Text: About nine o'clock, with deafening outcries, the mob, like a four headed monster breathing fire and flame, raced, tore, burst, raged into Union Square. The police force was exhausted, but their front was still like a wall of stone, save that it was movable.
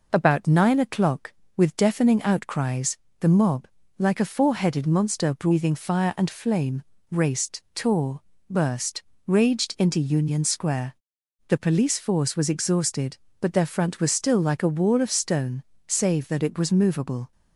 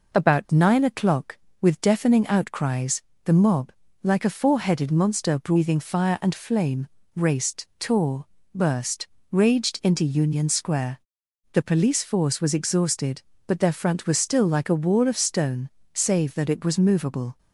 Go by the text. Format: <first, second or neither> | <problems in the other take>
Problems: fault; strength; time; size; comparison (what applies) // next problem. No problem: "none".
neither | none